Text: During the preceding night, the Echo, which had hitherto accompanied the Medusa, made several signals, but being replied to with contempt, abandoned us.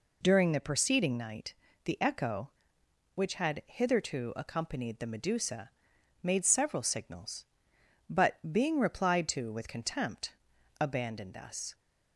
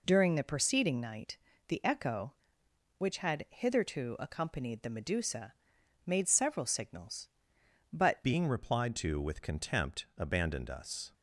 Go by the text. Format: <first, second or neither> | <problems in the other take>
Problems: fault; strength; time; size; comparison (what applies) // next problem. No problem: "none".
first | changes voice at "being"; from 8.2 s on; 2.9 s long